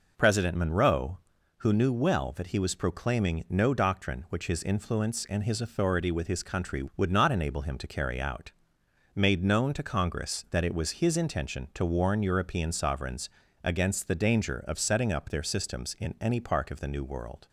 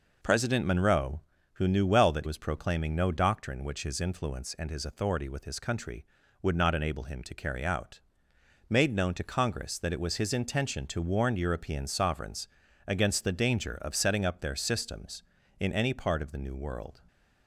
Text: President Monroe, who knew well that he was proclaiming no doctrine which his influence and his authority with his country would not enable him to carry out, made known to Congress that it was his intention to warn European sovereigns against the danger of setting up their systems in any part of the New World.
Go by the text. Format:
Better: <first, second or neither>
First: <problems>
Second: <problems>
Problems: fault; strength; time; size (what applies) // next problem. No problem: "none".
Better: first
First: pauses between "sovereigns" and "against"; slight; at 13.2 s; 0.36 s long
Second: skips "he"; at 2.2 s // pauses between "sovereigns" and "against"; at 12.4 s; 0.40 s long